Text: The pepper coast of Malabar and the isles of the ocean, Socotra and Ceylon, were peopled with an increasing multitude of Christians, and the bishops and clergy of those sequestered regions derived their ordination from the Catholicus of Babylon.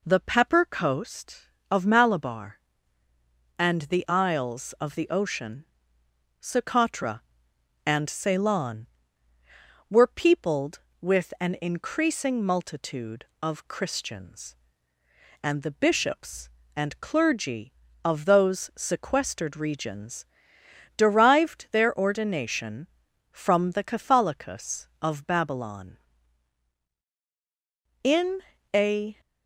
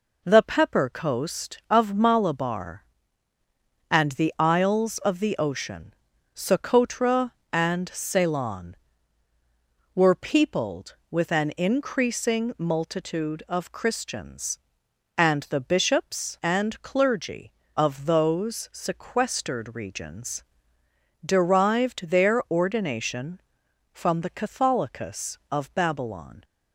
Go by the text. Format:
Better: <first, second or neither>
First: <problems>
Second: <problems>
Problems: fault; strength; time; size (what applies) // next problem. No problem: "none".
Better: second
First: pauses between "regions" and "derived"; noticeable; at 20.2 s; 0.72 s long // goes on to say "In a"; noticeable; from 28.0 s on; 1.1 s long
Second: pauses between "regions" and "derived"; noticeable; at 20.4 s; 0.82 s long